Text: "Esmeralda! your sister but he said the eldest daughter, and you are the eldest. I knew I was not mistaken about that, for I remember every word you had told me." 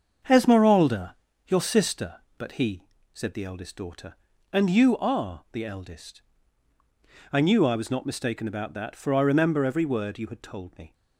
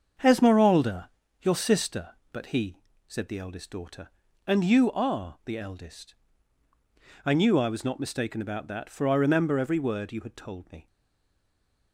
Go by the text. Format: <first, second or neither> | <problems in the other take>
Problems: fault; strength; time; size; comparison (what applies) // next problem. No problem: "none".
first | starts louder than the rest; until 1.5 s; 7 dB; also in the first // pauses between "he" and "said"; slight; at 2.7 s; 0.28 s long; slight in the first // stays silent after the last word; from 10.8 s on; 1.1 s long